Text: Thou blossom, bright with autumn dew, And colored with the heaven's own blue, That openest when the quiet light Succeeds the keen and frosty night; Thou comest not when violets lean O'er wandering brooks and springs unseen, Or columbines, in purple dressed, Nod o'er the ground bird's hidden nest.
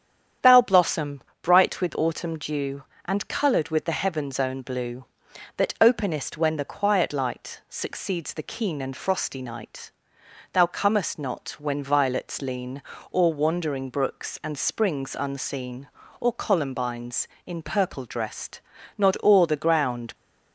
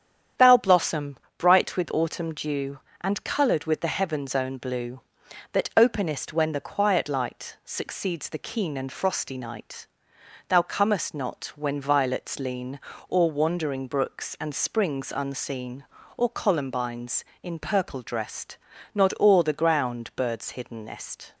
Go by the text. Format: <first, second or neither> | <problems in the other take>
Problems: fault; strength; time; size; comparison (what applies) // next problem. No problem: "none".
second | starts louder than the rest; strong; until 1.6 s; 9.5 dB; strong in the second // pauses between "lean" and "O'er"; slight; at 12.8 s; 0.30 s long; slight in the second // stops before "bird's hidden nest"; at 20.1 s